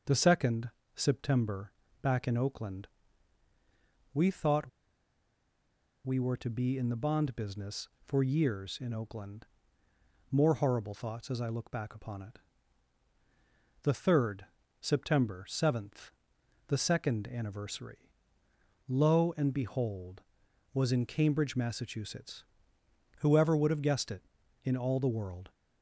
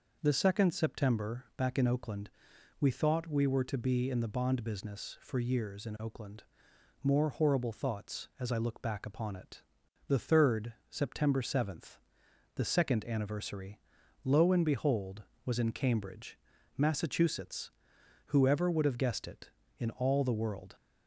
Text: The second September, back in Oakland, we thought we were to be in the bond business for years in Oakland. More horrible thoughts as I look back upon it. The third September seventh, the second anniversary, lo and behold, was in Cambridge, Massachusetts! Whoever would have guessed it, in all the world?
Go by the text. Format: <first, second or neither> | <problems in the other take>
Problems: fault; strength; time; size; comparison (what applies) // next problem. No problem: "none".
second | starts louder than the rest; until 1.3 s; 6.5 dB // pauses between "second" and "September"; slight; at 0.7 s; 0.24 s long // pauses between "thought" and "we"; strong; at 4.6 s; 1.3 s long // pauses between "third" and "September"; slight; at 14.4 s; 0.34 s long; slight in the second